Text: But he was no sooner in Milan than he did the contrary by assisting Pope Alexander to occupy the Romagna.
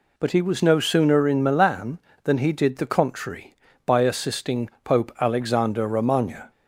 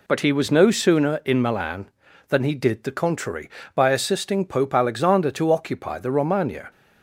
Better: second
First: skips "to occupy the"; at 5.8 s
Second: none

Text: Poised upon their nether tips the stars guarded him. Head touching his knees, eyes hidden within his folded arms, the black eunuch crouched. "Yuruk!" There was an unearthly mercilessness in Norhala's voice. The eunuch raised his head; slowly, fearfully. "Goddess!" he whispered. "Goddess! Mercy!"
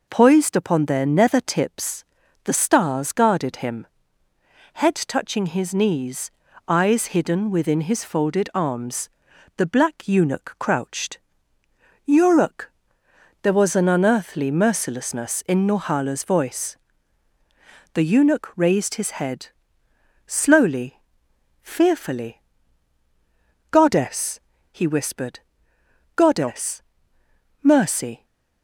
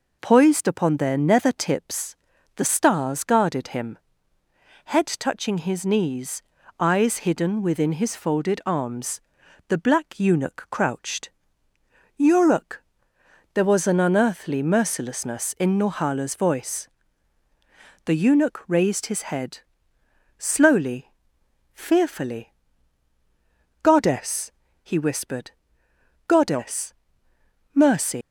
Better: first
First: pauses between "tips" and "the"; at 2.0 s; 0.40 s long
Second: pauses between "tips" and "the"; at 2.1 s; 0.40 s long // leaves "Mercy" unfinished; at 28.2 s; 150 ms

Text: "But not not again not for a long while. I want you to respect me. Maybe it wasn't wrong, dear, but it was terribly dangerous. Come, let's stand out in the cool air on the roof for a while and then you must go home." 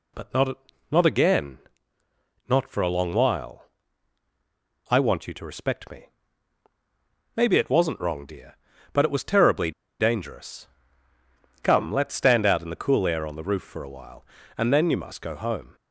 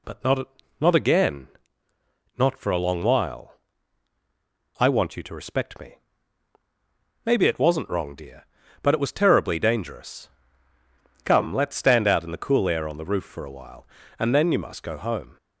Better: second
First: pauses between "not" and "not"; slight; at 0.5 s; 0.36 s long // pauses between "again" and "not"; noticeable; at 1.5 s; 0.90 s long // pauses between "terribly" and "dangerous"; slight; at 9.7 s; 0.27 s long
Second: pauses between "not" and "not"; slight; at 0.4 s; 0.34 s long // pauses between "again" and "not"; noticeable; at 1.4 s; 0.90 s long

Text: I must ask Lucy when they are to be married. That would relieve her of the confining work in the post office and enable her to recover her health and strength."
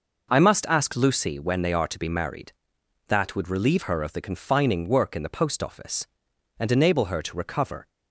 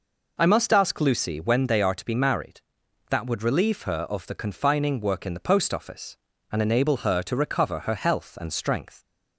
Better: second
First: stops before "her health and strength"; at 7.8 s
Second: none

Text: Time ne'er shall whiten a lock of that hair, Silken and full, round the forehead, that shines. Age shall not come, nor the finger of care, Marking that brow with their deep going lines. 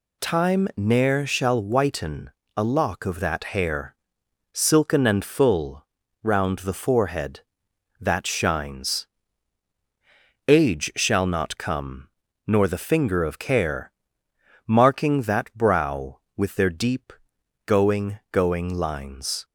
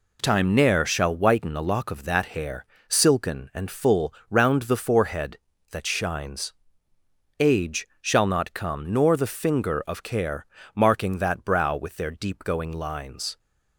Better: second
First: pauses between "whiten" and "a"; slight; at 2.3 s; 0.26 s long // pauses between "deep" and "going"; noticeable; at 17.1 s; 0.54 s long // says "going" twice; at 18.3 s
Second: none

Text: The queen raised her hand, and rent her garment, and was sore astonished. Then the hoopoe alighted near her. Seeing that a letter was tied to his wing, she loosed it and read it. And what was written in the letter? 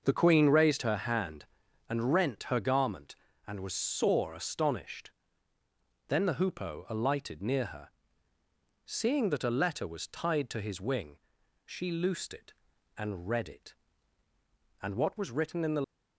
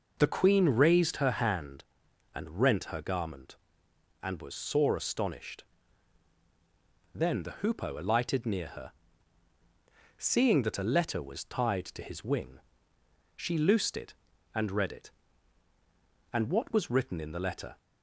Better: second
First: starts louder than the rest; until 1.0 s; 6 dB // stops before "letter"; at 15.8 s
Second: none

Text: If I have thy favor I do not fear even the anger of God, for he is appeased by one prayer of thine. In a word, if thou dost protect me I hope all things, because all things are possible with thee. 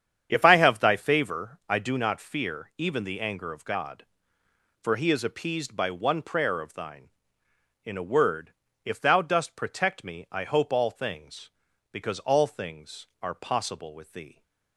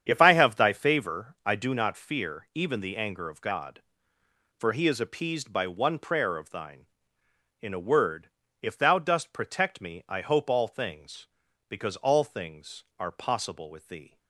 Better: neither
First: starts louder than the rest; strong; until 1.3 s; 8.5 dB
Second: starts louder than the rest; strong; until 1.0 s; 8.5 dB

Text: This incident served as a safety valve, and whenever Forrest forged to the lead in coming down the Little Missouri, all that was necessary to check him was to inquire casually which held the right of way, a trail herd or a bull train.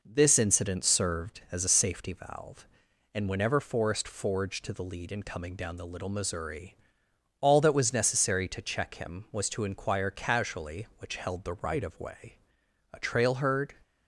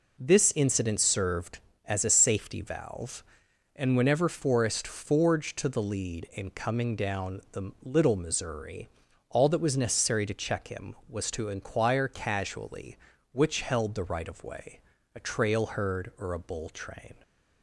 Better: second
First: stops before "or a bull train"; at 13.8 s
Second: none

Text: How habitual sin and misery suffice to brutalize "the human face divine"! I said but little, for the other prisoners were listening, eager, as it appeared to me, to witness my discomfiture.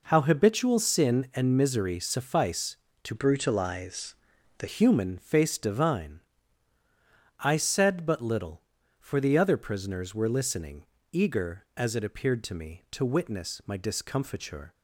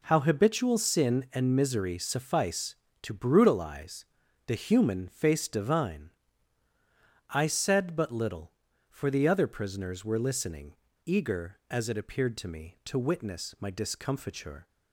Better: second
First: changes voice from "brutalize" to "the"; from 3.1 to 4.6 s; 1.5 s long // pauses between "brutalize" and "the"; at 4.1 s; 0.42 s long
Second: pauses between "brutalize" and "the"; at 4.0 s; 0.44 s long

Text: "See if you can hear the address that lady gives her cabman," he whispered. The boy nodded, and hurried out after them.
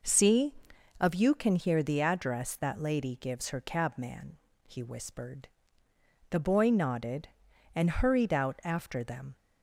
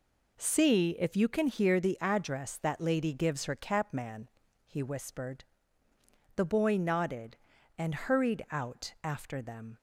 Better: second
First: says "of" for "if"; at 0.9 s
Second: none

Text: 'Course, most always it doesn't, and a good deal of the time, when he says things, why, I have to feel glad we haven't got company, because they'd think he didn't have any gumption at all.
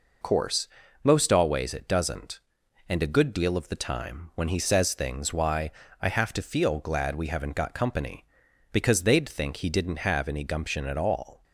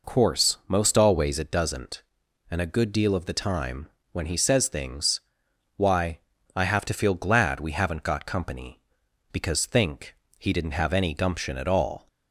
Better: first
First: none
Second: skips "they'd"; at 9.6 s // pauses between "think" and "he"; slight; at 10.1 s; 0.22 s long

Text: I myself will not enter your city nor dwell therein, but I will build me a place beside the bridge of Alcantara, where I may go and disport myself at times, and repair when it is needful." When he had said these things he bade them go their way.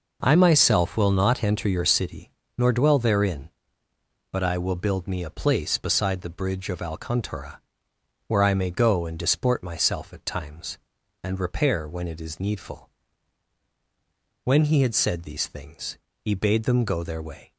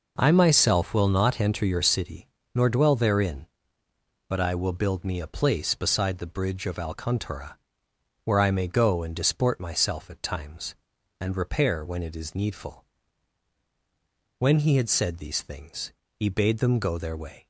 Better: neither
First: pauses between "city" and "nor"; slight; at 2.3 s; 0.28 s long // pauses between "things" and "he"; slight; at 15.9 s; 0.24 s long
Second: pauses between "city" and "nor"; slight; at 2.2 s; 0.28 s long // pauses between "things" and "he"; slight; at 15.9 s; 0.24 s long

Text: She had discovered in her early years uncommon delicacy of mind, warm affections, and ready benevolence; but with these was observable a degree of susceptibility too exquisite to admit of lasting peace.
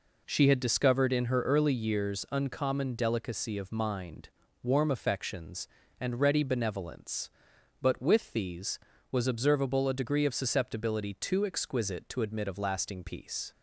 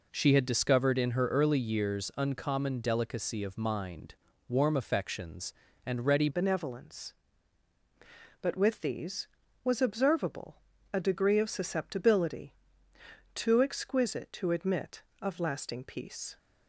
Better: first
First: none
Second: changes voice at "benevolence"; from 6.3 s on; 10.0 s long // pauses between "observable" and "a"; slight; at 10.5 s; 0.36 s long // pauses between "susceptibility" and "too"; noticeable; at 12.5 s; 0.82 s long

